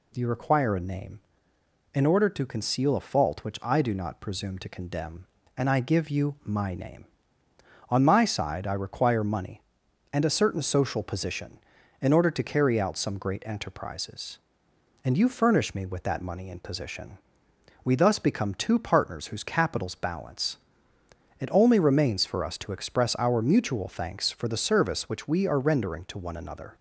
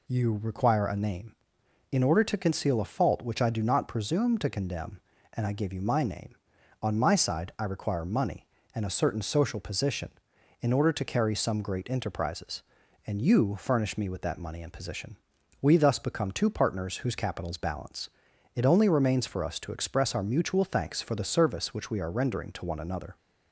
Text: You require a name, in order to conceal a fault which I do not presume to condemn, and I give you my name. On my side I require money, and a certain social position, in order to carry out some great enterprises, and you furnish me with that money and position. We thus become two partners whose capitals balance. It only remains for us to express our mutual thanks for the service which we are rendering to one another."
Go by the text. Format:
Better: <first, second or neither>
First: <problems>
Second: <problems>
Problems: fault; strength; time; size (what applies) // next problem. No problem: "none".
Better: first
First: none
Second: skips "out"; at 11.3 s